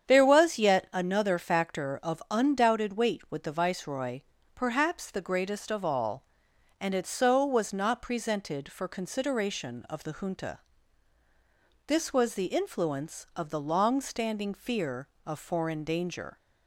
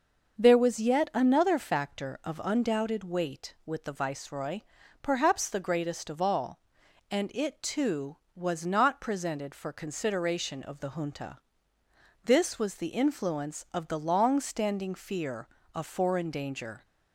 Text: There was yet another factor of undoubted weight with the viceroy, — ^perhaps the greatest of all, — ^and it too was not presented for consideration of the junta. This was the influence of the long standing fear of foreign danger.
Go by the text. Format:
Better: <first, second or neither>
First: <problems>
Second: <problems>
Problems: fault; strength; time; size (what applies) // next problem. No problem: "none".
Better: second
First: starts louder than the rest; strong; until 1.1 s; 8.5 dB // says "so" for "too"; at 7.0 s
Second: starts louder than the rest; until 1.4 s; 6.5 dB